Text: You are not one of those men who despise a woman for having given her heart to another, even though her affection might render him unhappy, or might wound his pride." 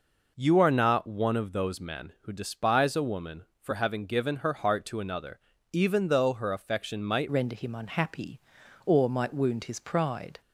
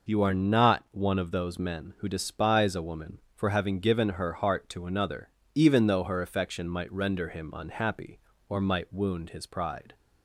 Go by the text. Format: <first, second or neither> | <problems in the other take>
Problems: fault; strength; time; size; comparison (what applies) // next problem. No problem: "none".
second | changes voice at "render"; from 7.2 s on; 3.2 s long